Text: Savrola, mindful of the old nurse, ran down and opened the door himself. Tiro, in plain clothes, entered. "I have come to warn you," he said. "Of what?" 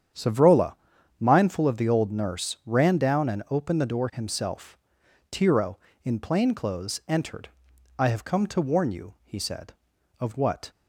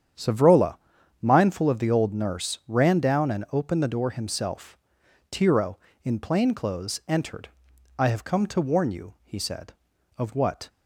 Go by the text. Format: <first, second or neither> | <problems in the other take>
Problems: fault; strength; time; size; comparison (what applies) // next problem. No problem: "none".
neither | starts louder than the rest; strong; the same in both